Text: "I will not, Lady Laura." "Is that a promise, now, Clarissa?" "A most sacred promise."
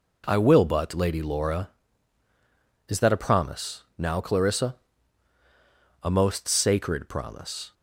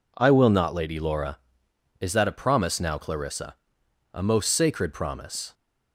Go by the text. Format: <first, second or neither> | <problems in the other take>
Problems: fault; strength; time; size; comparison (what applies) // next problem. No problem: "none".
second | says "but" for "not"; at 0.6 s